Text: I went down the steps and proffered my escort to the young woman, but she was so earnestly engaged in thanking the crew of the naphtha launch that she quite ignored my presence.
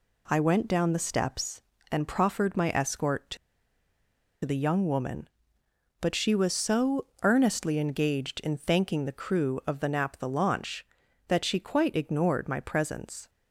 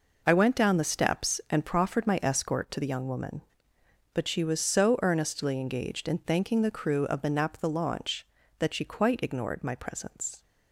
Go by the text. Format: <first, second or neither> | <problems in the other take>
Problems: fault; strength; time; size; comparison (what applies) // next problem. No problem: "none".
second | pauses between "to" and "the"; at 3.3 s; 1.0 s long // pauses between "so" and "earnestly"; slight; at 7.0 s; 0.18 s long